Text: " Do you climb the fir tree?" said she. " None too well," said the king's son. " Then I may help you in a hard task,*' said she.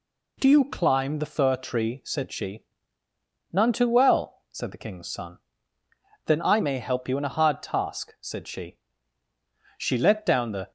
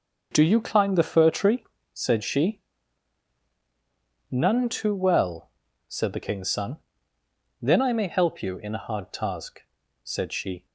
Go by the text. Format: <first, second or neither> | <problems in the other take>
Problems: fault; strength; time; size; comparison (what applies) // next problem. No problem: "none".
second | goes on to say "She let down the"; noticeable; from 9.7 s on; 0.94 s long